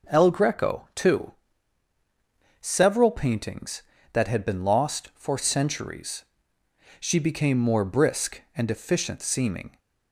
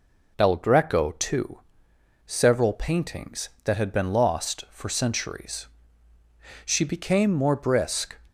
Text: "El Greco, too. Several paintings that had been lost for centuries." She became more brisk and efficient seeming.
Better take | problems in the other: first | stops before "and efficient seeming"; at 8.2 s

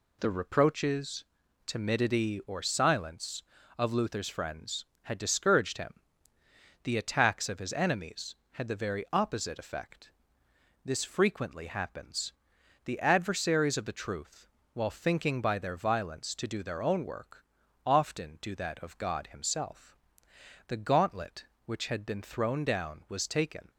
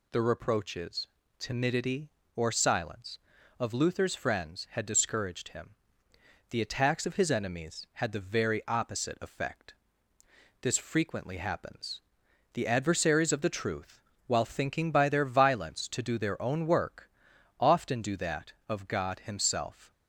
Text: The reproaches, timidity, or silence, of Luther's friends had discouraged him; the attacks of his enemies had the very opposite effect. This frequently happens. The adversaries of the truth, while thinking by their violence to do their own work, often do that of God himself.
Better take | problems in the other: second | goes on to say "The gauntlet which had been thrown down was taken"; strong; from 20.6 s on; 3.0 s long

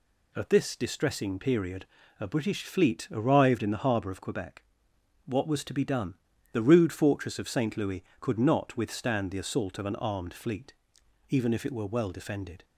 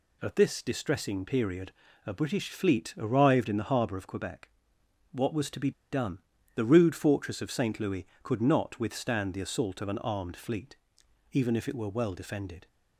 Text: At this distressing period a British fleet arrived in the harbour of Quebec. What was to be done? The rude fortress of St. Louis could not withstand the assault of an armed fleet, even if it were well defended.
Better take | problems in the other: first | pauses between "period" and "a"; slight; at 1.7 s; 0.34 s long; slight in the first // pauses between "be" and "done"; slight; at 5.7 s; 0.20 s long

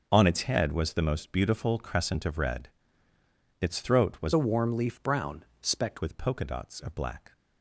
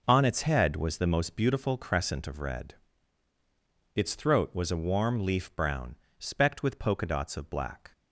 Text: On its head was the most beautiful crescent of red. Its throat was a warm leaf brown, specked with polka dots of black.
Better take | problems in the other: second | changes voice from "a" to "specked"; from 4.3 to 6.0 s; 1.7 s long

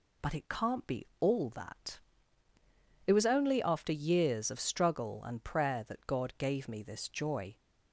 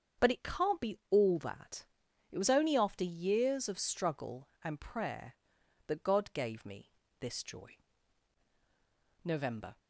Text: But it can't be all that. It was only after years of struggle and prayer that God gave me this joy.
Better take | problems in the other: first | starts louder than the rest; strong; until 1.3 s; 7.5 dB // pauses between "me" and "this"; slight; at 6.9 s; 0.28 s long // goes on to say "NOVEMBER"; from 9.2 s on; 0.56 s long

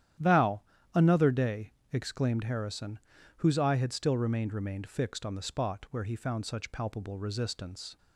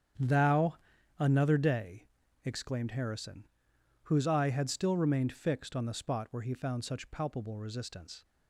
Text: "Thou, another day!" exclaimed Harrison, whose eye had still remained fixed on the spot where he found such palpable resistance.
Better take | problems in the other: second | starts louder than the rest; strong; until 1.5 s; 11 dB; strong in the second // says "remained" twice; at 4.5 s

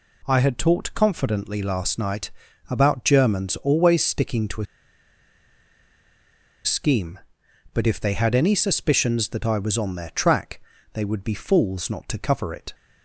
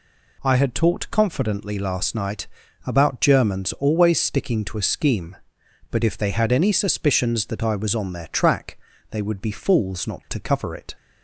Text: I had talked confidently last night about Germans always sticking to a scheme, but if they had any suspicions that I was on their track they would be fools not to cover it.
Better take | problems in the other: second | pauses between "night" and "about"; at 2.3 s; 0.38 s long; also in the second // pauses between "a" and "scheme"; strong; at 4.6 s; 1.9 s long // pauses between "track" and "they"; slight; at 10.6 s; 0.32 s long; slight in the second

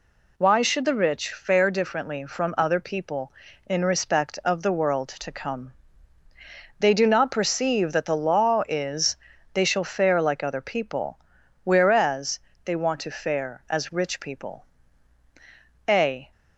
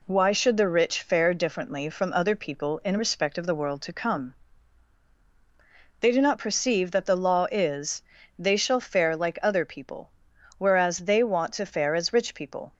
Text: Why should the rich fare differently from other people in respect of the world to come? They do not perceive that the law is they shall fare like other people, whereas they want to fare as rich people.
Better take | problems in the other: second | pauses between "is" and "they"; at 9.1 s; 0.38 s long; also in the second // pauses between "whereas" and "they"; slight; at 12.3 s; 0.24 s long // goes on to say "A"; slight; from 15.8 s on; 0.44 s long

